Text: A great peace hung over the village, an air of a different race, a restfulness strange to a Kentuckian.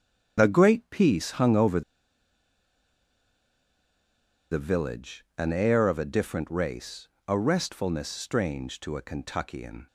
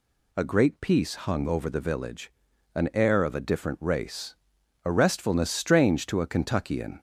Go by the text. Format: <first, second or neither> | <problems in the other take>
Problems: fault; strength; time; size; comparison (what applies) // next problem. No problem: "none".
second | starts louder than the rest; strong; until 1.4 s; 8 dB // pauses between "over" and "the"; strong; at 1.8 s; 2.7 s long